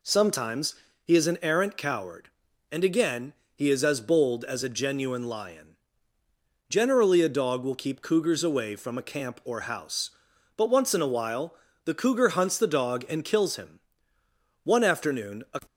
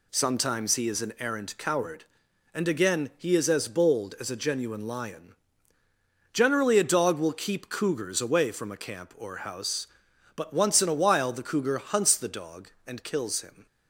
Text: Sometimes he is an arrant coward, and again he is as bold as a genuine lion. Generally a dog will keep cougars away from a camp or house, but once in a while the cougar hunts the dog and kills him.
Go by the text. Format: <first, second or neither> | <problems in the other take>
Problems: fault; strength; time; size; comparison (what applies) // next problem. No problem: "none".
second | pauses between "Sometimes" and "he"; slight; at 0.7 s; 0.30 s long // pauses between "again" and "he"; slight; at 3.3 s; 0.20 s long // pauses between "while" and "the"; slight; at 11.5 s; 0.30 s long // goes on to say "One afternoon a"; noticeable; from 14.6 s on; 0.96 s long